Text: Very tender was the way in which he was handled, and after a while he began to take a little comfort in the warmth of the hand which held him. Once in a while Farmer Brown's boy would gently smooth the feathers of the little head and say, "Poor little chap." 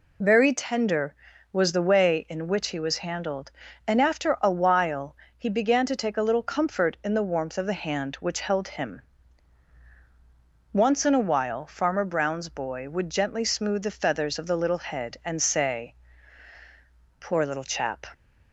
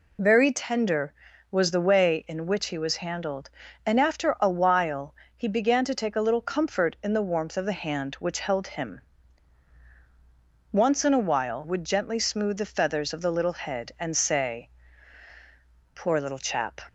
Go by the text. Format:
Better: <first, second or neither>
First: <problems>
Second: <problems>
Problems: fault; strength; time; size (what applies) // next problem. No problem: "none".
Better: first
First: pauses between "while" and "he"; slight; at 5.1 s; 0.20 s long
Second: pauses between "while" and "he"; slight; at 5.1 s; 0.20 s long // skips "Farmer Brown's boy"; at 11.6 s